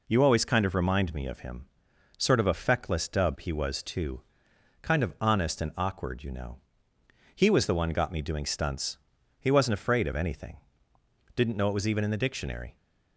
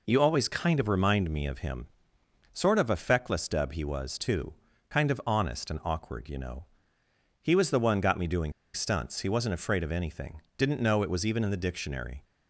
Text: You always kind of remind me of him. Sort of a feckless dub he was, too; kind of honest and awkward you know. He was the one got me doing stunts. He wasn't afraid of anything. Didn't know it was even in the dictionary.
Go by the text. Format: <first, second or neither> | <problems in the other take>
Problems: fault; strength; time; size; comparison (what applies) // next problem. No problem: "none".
first | pauses between "doing" and "stunts"; slight; at 8.5 s; 0.22 s long